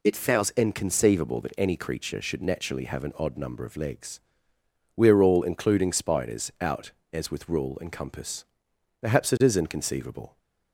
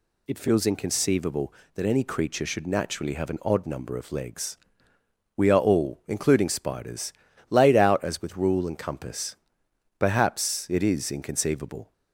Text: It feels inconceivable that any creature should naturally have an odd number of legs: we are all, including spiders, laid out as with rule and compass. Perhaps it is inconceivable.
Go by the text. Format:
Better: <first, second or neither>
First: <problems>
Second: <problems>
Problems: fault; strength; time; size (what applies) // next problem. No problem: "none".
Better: second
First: skips "laid"; at 6.5 s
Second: none